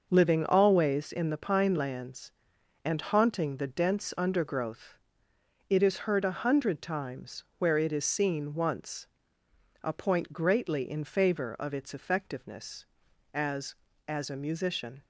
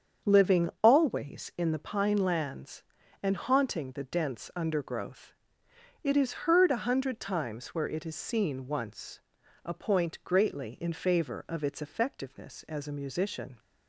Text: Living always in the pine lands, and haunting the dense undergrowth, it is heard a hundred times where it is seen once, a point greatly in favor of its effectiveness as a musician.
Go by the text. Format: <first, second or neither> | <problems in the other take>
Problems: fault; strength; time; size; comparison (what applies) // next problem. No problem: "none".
second | starts louder than the rest; noticeable; until 1.1 s; 6 dB; strong in the second // pauses between "times" and "where"; slight; at 7.4 s; 0.16 s long // says "as" twice; at 14.0 s